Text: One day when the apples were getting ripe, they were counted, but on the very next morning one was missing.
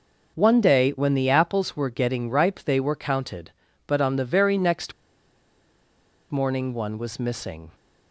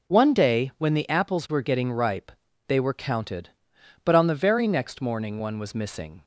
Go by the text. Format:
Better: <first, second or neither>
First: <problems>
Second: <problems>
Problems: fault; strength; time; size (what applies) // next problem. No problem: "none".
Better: second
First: pauses between "next" and "morning"; strong; at 4.9 s; 1.3 s long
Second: none